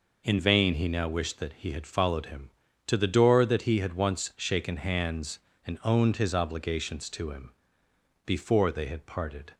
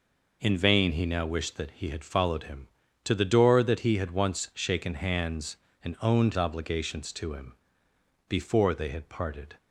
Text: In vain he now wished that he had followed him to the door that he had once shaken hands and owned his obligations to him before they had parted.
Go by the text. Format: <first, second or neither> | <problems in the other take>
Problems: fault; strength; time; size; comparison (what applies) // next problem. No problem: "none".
first | skips "his"; at 6.3 s // pauses between "him" and "before"; noticeable; at 7.5 s; 0.74 s long; noticeable in the first